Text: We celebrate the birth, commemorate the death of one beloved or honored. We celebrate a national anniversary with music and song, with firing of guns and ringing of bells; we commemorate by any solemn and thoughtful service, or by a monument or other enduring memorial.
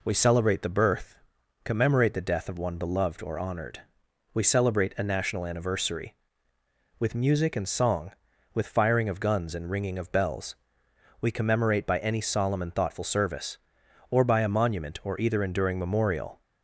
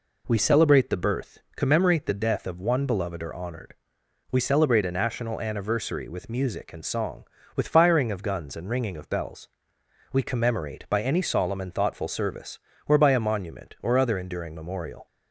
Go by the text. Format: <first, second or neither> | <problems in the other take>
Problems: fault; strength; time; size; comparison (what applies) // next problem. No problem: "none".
second | says "either" for "other"; at 15.2 s